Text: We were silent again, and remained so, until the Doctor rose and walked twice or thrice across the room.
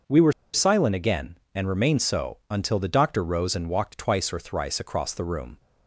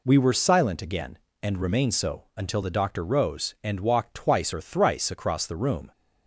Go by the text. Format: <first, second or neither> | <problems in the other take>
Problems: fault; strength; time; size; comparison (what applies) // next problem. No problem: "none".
second | starts louder than the rest; until 1.2 s; 6 dB // pauses between "were" and "silent"; slight; at 0.3 s; 0.21 s long